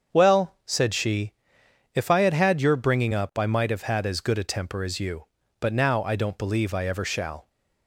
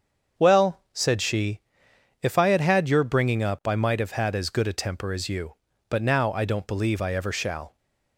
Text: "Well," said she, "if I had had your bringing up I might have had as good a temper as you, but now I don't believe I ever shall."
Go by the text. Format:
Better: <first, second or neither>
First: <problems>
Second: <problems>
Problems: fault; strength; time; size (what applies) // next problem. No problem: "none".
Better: neither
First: starts louder than the rest; until 1.2 s; 7 dB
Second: starts louder than the rest; until 1.4 s; 7 dB